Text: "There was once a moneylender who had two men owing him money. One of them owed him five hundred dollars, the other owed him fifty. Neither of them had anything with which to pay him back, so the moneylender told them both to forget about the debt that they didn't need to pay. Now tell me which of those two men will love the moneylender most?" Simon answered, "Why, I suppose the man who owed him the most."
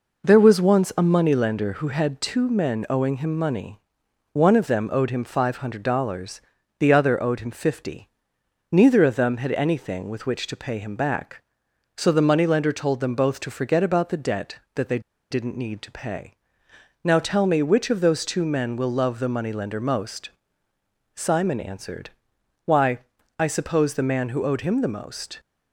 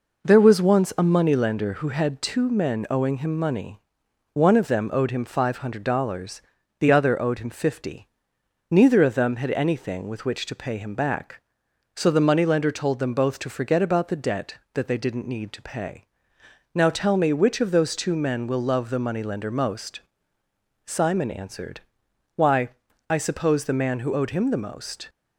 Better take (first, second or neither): second